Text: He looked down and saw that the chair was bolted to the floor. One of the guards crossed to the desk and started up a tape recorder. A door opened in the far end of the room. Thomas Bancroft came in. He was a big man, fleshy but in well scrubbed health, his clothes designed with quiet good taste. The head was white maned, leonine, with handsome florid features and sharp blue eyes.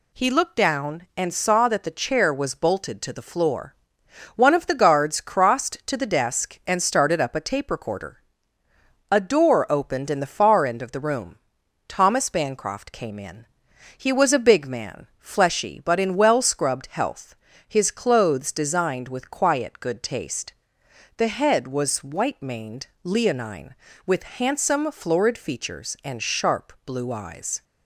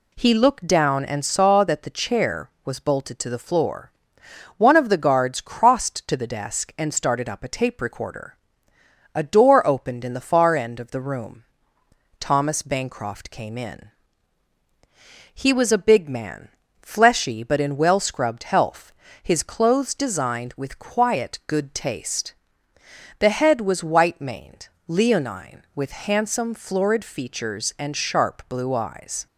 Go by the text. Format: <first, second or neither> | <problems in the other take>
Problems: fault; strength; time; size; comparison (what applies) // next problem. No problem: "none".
neither | none